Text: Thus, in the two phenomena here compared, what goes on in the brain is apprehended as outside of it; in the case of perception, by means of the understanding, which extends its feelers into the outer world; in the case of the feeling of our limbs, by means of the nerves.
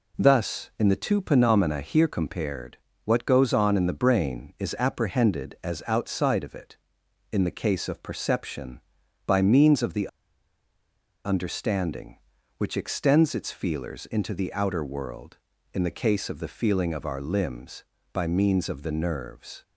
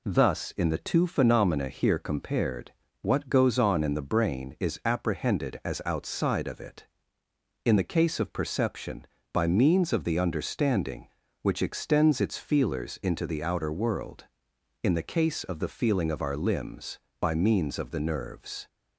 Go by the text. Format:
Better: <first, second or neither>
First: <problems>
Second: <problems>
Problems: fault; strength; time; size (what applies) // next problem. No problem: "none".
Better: second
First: pauses between "the" and "understanding"; at 10.0 s; 1.1 s long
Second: none